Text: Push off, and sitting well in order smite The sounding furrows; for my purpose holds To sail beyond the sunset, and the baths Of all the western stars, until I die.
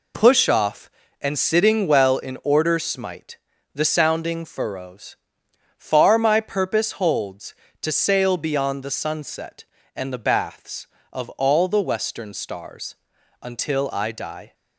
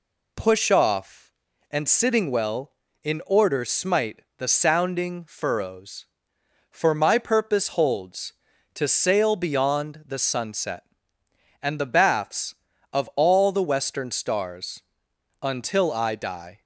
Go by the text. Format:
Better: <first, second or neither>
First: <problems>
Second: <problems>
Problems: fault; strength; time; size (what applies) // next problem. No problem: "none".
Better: second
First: pauses between "smite" and "The"; at 3.3 s; 0.38 s long // says "far" for "for"; at 5.7 s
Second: pauses between "smite" and "The"; slight; at 4.2 s; 0.16 s long